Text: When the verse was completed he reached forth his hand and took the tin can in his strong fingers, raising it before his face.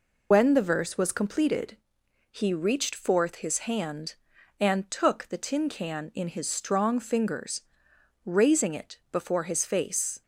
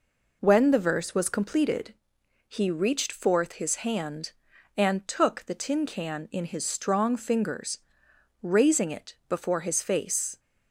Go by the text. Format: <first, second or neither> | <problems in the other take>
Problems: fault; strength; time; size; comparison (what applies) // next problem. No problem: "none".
second | loses the start of "When"; at 0.3 s; 65 ms // pauses between "completed" and "he"; noticeable; at 1.7 s; 0.54 s long; noticeable in the second